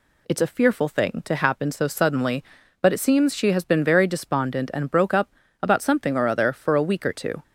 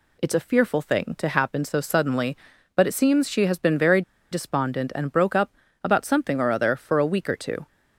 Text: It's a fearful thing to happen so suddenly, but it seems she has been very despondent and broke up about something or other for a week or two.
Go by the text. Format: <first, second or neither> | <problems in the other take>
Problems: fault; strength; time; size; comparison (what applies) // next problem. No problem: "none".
first | pauses between "very" and "despondent"; slight; at 4.0 s; 0.30 s long // pauses between "up" and "about"; slight; at 5.5 s; 0.30 s long; slight in the first